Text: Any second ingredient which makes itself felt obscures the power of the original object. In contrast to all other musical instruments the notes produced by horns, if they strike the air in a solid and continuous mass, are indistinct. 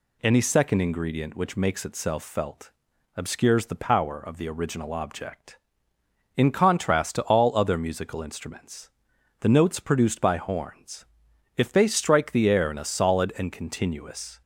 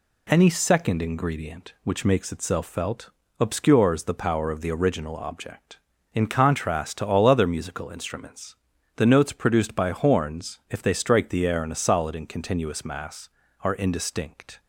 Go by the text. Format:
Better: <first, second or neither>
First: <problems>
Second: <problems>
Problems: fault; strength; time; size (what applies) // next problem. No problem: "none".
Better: second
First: pauses between "felt" and "obscures"; at 2.7 s; 0.44 s long // pauses between "instruments" and "the"; noticeable; at 8.8 s; 0.52 s long // stops before "mass are indistinct"; at 14.4 s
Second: pauses between "felt" and "obscures"; slight; at 3.0 s; 0.32 s long // pauses between "instruments" and "the"; at 8.5 s; 0.42 s long